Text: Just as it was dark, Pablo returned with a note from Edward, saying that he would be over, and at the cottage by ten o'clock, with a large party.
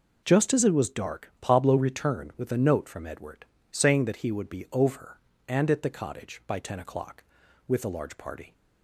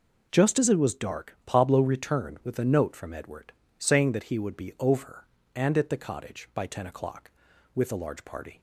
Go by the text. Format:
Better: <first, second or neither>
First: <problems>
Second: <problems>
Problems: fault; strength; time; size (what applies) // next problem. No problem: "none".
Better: neither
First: none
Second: none